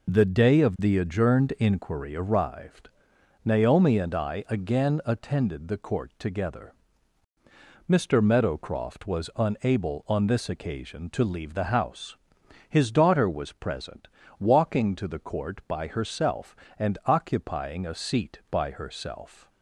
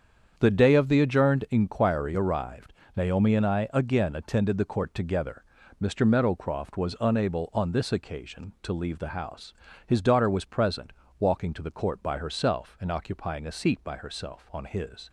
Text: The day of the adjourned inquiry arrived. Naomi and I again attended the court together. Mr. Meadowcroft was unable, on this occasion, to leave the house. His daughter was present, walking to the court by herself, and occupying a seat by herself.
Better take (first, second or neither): first